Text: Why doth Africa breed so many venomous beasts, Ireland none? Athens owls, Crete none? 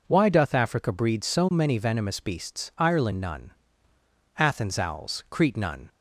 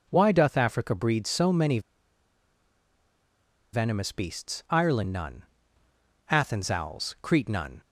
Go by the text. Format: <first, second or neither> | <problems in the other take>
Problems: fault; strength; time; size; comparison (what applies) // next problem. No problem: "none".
first | pauses between "many" and "venomous"; strong; at 1.7 s; 1.9 s long